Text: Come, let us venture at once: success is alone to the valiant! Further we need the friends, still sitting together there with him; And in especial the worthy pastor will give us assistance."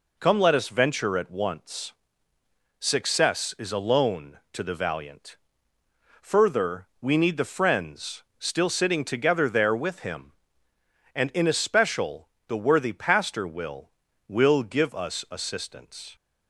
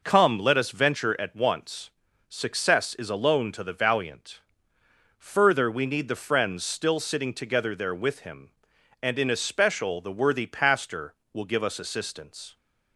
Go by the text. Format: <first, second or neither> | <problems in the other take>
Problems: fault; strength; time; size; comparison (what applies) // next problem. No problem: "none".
second | pauses between "especial" and "the"; slight; at 12.2 s; 0.18 s long // says "will" twice; at 14.2 s